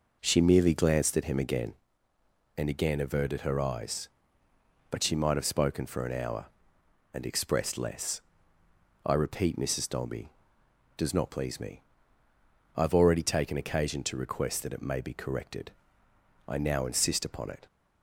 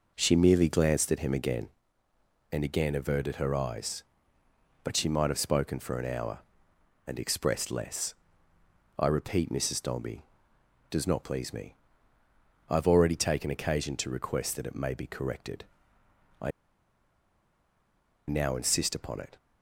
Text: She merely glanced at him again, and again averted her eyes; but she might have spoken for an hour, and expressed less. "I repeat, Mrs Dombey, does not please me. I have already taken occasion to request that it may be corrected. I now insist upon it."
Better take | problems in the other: first | pauses between "I" and "now"; strong; at 16.5 s; 1.7 s long

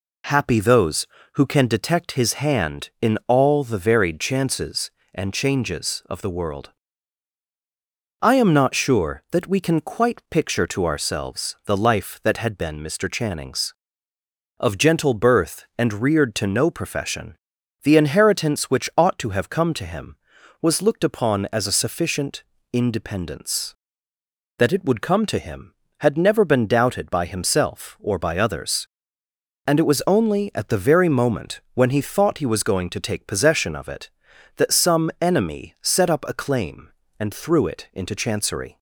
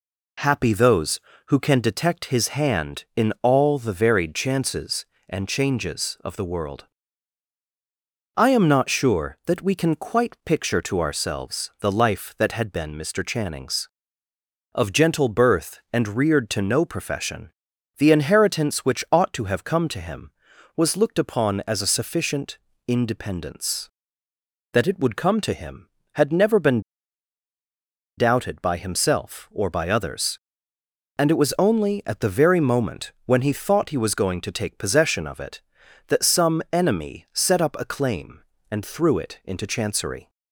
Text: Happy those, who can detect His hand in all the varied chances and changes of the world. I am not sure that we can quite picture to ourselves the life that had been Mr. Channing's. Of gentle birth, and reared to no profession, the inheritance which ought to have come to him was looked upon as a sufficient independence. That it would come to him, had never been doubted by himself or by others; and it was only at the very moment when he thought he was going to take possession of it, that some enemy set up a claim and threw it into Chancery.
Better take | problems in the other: first | pauses between "sufficient" and "independence"; slight; at 22.5 s; 0.28 s long; slight in the first // pauses between "been" and "doubted"; strong; at 26.8 s; 1.3 s long

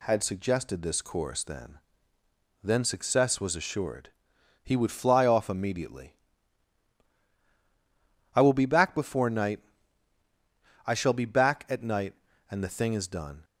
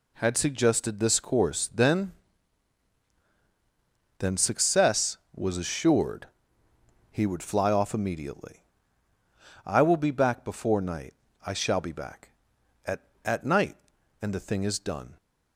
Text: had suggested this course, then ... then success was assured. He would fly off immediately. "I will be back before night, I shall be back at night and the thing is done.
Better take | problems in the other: first | says "at" twice; at 13.2 s

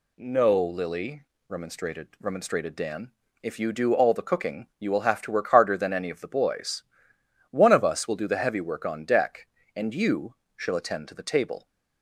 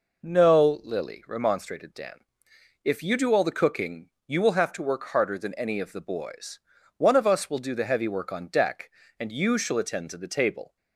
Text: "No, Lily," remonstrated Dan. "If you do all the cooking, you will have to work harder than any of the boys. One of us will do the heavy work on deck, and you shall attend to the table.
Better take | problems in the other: second | says "remonstrated" twice; at 2.1 s // pauses between "you" and "shall"; slight; at 10.3 s; 0.20 s long

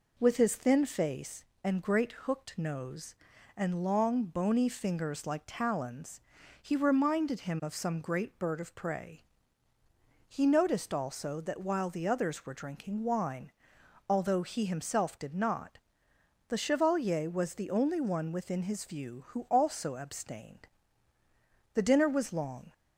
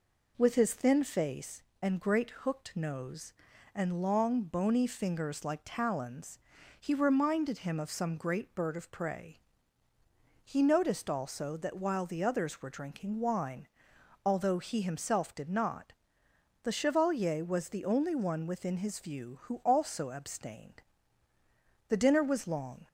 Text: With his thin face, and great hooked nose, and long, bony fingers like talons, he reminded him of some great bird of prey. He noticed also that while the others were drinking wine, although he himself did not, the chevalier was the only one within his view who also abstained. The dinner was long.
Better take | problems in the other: neither | none

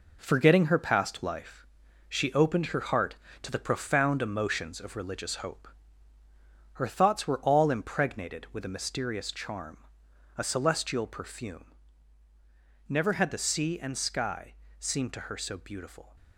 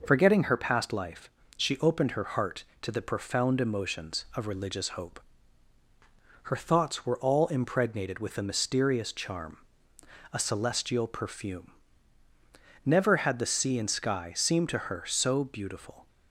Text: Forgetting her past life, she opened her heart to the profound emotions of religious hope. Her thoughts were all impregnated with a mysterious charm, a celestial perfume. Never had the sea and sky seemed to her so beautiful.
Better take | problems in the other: second | gets quieter; throughout; 7 dB // pauses between "sky" and "seemed"; slight; at 14.5 s; 0.24 s long

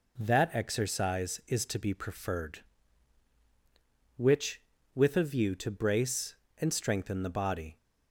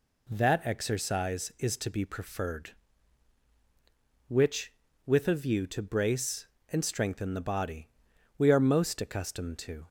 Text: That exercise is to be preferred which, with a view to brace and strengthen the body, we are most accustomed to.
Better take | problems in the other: second | stops before "we are most accustomed to"; at 7.7 s

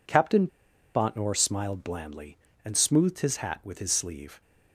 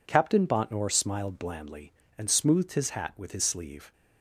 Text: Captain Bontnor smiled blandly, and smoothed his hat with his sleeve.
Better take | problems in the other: second | pauses between "Captain" and "Bontnor"; noticeable; at 0.4 s; 0.47 s long

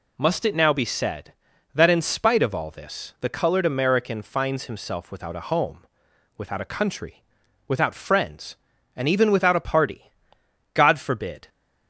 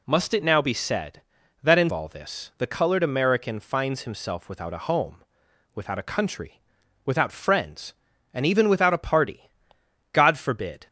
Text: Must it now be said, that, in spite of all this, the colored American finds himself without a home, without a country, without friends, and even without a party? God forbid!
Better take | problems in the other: first | skips "spite of"; at 1.9 s

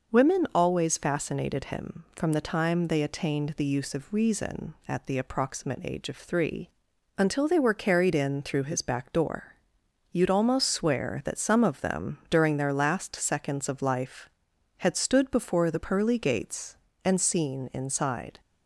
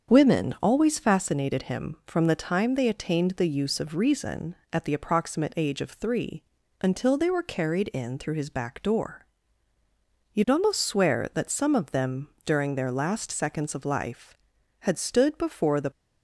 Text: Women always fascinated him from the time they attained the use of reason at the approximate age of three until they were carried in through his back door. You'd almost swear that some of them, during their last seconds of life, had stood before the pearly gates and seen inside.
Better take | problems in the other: first | starts louder than the rest; strong; until 1.1 s; 7 dB // pauses between "three" and "until"; at 6.4 s; 0.40 s long; noticeable in the first // stops before "pearly gates and seen inside"; at 15.9 s

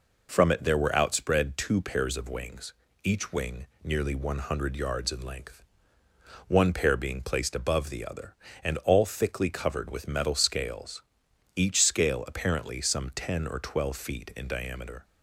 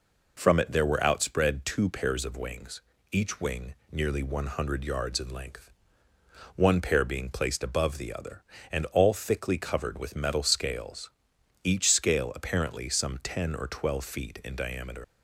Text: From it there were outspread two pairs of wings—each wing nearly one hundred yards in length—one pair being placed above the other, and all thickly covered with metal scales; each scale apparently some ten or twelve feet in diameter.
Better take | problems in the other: first | pauses between "wing" and "nearly"; slight; at 3.7 s; 0.16 s long; slight in the first // leaves "diameter" unfinished; at 15.0 s; 75 ms

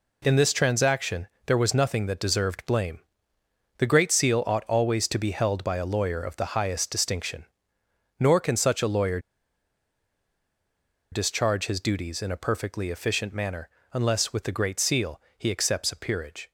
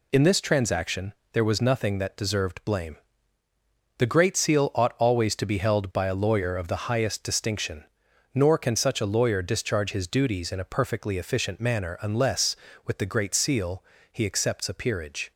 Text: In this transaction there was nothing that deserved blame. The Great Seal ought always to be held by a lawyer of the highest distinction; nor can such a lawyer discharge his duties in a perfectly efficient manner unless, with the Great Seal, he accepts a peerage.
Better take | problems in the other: second | pauses between "transaction" and "there"; slight; at 1.2 s; 0.20 s long; slight in the second // pauses between "lawyer" and "discharge"; strong; at 9.1 s; 1.9 s long // pauses between "manner" and "unless"; slight; at 13.6 s; 0.26 s long

